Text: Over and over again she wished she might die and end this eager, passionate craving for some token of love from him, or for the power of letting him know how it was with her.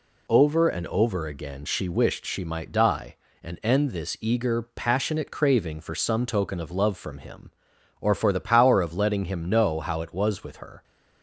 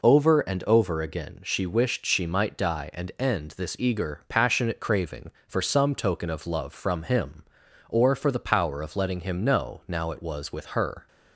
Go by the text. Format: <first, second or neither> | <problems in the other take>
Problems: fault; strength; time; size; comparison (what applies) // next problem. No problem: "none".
first | says "now" for "how"; at 9.8 s